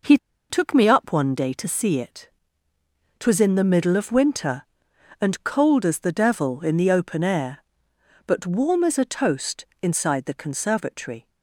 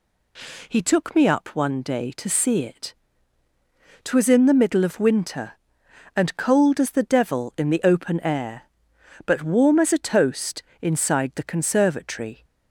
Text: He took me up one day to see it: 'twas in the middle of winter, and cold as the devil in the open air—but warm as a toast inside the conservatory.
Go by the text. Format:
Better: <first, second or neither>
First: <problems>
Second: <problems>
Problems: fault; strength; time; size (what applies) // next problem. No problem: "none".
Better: second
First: pauses between "He" and "took"; slight; at 0.1 s; 0.31 s long // pauses between "toast" and "inside"; slight; at 9.6 s; 0.16 s long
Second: pauses between "toast" and "inside"; slight; at 10.6 s; 0.18 s long